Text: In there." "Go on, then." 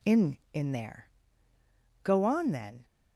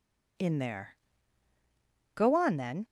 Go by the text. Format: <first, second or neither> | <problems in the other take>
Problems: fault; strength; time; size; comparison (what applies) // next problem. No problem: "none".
second | says "In" twice; at 0.5 s